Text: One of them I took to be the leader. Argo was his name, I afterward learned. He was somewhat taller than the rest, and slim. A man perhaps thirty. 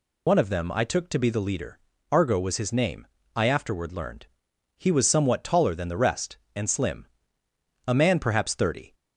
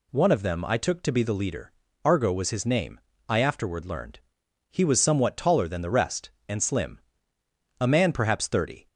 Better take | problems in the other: second | loses the start of "One"; at 0.2 s; 90 ms

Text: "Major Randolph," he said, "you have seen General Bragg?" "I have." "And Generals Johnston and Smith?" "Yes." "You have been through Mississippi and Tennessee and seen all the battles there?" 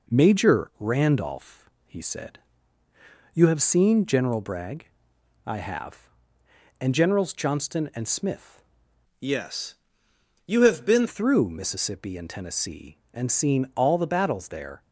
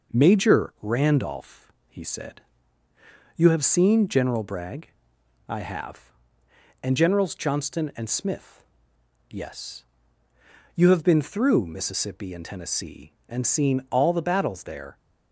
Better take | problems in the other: second | changes voice from "Yes" to "been"; from 9.2 to 11.0 s; 1.8 s long

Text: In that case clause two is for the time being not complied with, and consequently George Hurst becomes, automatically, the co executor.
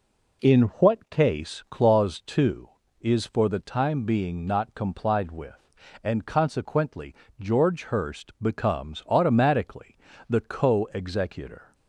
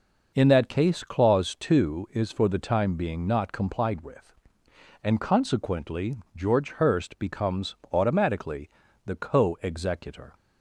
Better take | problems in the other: second | says "what" for "that"; at 0.8 s // pauses between "consequently" and "George"; slight; at 7.1 s; 0.24 s long; slight in the second

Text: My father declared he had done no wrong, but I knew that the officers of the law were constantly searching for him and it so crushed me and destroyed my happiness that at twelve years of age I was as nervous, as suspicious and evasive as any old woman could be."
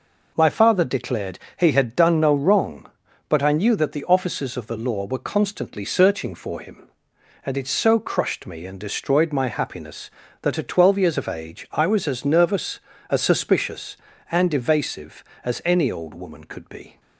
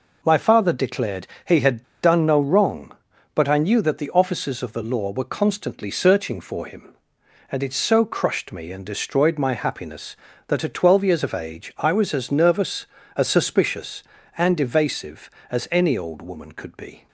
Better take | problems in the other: first | pauses between "declared" and "he"; slight; at 1.2 s; 0.22 s long; slight in the first // pauses between "had" and "done"; slight; at 1.8 s; 0.20 s long

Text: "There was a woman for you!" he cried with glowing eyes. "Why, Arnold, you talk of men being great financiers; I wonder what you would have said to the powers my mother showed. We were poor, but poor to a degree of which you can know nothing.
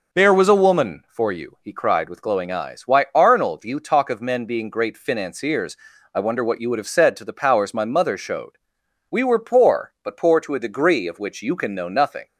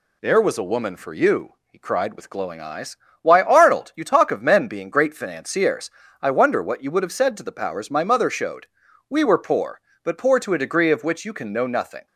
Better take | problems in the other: neither | none

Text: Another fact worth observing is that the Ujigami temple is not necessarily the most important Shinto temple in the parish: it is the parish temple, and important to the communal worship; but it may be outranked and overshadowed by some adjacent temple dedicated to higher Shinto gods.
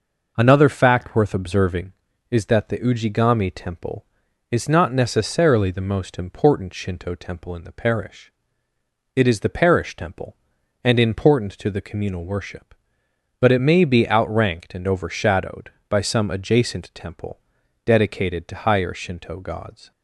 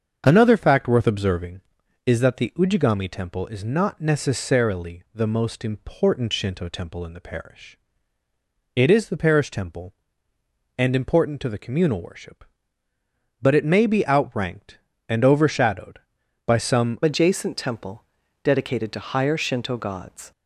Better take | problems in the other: first | starts louder than the rest; until 1.2 s; 7 dB // changes voice at "adjacent"; from 17.0 s on; 3.3 s long // pauses between "temple" and "dedicated"; at 18.0 s; 0.40 s long; also in the first

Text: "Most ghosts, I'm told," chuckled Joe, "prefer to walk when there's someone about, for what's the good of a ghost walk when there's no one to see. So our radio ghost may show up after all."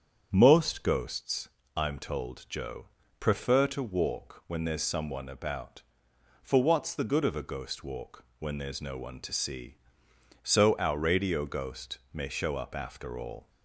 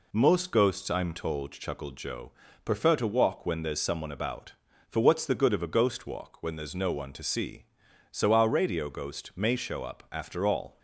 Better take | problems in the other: second | starts louder than the rest; strong; until 1.3 s; 8 dB // skips "chuckled"; at 2.4 s // pauses between "walk" and "when"; slight; at 8.2 s; 0.16 s long

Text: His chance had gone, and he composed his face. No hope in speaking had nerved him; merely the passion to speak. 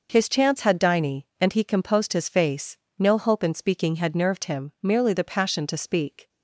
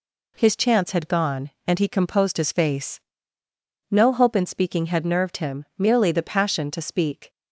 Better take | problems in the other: second | says "diny" for "gone"; at 0.7 s

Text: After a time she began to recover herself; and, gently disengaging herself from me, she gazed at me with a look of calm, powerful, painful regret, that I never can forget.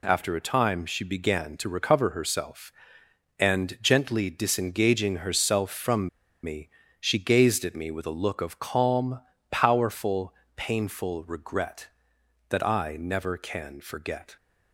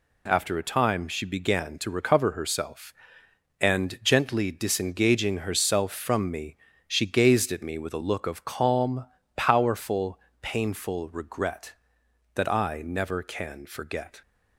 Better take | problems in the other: second | pauses between "from" and "me"; slight; at 6.0 s; 0.34 s long

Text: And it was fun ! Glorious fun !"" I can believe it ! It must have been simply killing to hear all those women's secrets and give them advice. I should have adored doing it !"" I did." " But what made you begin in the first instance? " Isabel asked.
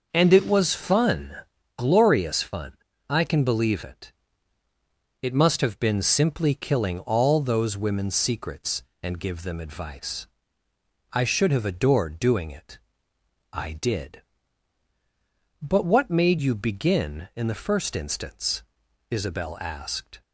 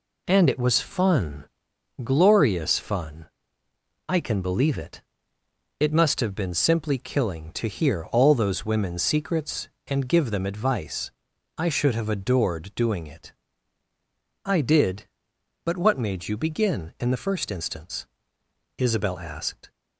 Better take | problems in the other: second | starts louder than the rest; noticeable; until 1.1 s; 6 dB // skips "to hear"; at 6.9 s

